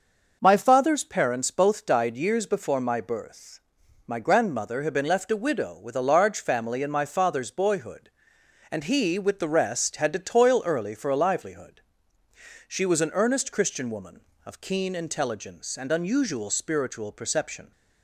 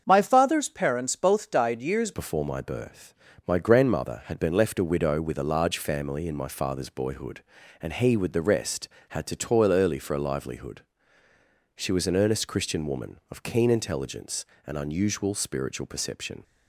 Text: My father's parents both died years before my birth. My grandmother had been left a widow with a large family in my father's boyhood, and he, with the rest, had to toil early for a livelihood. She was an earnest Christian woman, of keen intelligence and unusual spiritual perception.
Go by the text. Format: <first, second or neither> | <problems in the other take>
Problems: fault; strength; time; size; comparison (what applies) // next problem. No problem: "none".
first | starts louder than the rest; until 1.0 s; 7 dB // changes voice at "before"; from 2.1 s on; 14.3 s long